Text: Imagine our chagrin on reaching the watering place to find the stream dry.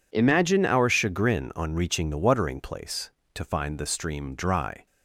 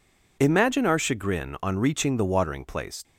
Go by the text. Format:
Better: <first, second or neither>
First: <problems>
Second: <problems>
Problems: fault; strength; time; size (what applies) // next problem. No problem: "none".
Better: first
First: none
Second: stops before "to find the stream dry"; at 3.0 s